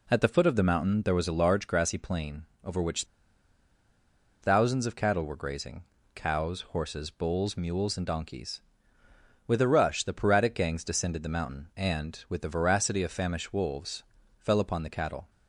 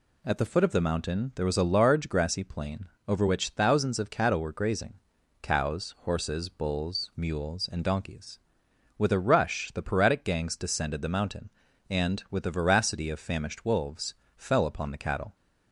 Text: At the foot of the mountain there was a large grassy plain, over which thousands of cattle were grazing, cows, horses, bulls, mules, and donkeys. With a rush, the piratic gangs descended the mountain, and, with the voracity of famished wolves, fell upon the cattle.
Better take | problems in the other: second | pauses between "which" and "thousands"; strong; at 3.0 s; 1.3 s long

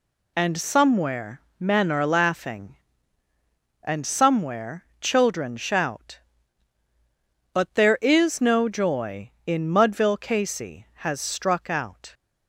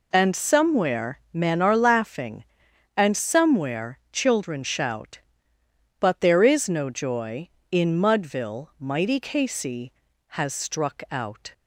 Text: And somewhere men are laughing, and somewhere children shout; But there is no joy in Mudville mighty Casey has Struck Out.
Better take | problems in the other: second | pauses between "somewhere" and "men"; slight; at 1.4 s; 0.18 s long // pauses between "somewhere" and "children"; slight; at 4.8 s; 0.16 s long // skips "mighty"; at 10.1 s

